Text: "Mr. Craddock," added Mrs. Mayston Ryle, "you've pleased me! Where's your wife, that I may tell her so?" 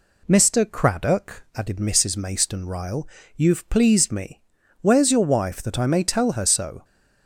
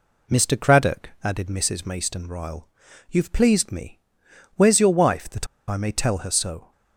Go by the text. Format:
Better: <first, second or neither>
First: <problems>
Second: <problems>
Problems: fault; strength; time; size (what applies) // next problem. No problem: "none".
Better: first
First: none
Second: pauses between "that" and "I"; slight; at 5.4 s; 0.24 s long